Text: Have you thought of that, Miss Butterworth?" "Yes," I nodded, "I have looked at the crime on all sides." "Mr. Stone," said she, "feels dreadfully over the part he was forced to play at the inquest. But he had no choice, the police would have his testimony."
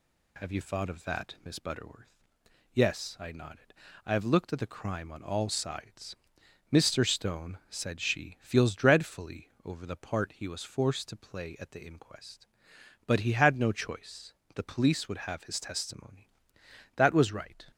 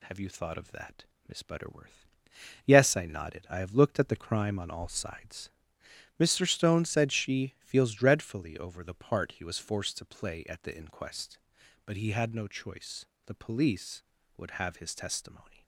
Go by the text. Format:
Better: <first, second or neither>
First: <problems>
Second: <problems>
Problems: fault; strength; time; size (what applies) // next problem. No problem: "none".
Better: second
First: pauses between "dreadfully" and "over"; slight; at 9.4 s; 0.16 s long // goes on to say "That was right"; noticeable; from 16.9 s on; 0.68 s long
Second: none